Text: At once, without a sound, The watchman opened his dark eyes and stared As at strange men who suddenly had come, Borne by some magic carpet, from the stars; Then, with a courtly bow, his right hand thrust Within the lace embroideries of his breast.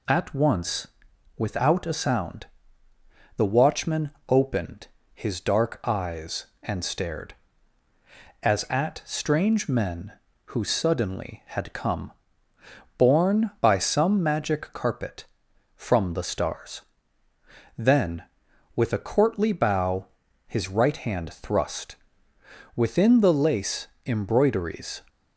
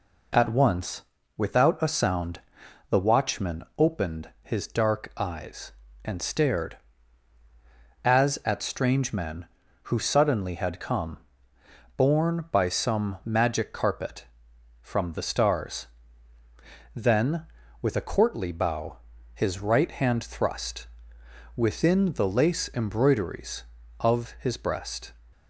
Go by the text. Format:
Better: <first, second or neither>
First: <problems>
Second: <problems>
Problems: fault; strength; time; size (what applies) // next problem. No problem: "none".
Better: second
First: pauses between "watchman" and "opened"; slight; at 4.1 s; 0.18 s long // pauses between "opened" and "his"; slight; at 4.8 s; 0.26 s long // pauses between "thrust" and "Within"; noticeable; at 21.9 s; 0.80 s long // pauses between "lace" and "embroideries"; slight; at 23.8 s; 0.18 s long // stops before "of his breast"; at 25.0 s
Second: pauses between "thrust" and "Within"; noticeable; at 20.8 s; 0.68 s long